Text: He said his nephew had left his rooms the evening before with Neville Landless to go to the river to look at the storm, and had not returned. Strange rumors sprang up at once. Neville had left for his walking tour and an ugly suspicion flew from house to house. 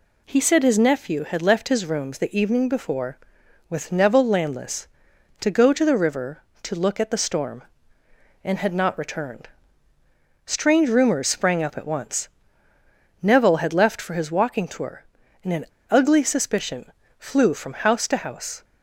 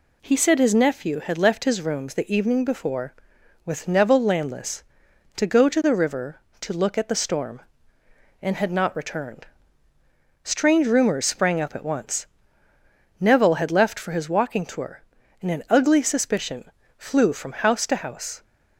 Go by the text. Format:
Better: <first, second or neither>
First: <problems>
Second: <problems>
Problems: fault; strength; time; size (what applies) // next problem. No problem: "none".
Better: second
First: pauses between "an" and "ugly"; slight; at 15.6 s; 0.24 s long // pauses between "suspicion" and "flew"; slight; at 16.9 s; 0.26 s long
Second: pauses between "suspicion" and "flew"; slight; at 16.7 s; 0.26 s long